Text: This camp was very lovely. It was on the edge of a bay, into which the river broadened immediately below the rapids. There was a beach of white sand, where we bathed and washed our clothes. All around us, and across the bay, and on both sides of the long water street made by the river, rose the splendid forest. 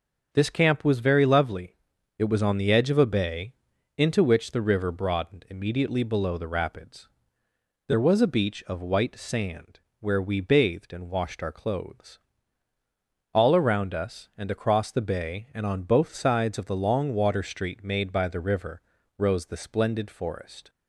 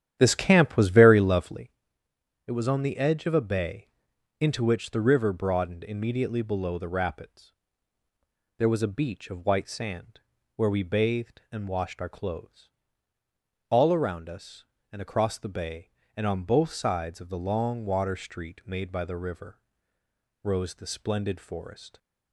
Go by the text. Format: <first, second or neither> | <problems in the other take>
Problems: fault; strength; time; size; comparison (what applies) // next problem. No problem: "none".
first | starts louder than the rest; strong; until 1.8 s; 10.5 dB